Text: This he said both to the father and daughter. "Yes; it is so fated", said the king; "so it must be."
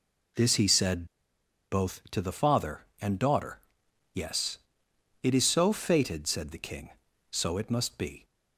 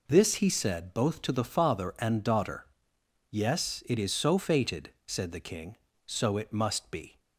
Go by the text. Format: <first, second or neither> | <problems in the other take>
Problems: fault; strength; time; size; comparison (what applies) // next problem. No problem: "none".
second | pauses between "said" and "both"; noticeable; at 1.0 s; 0.65 s long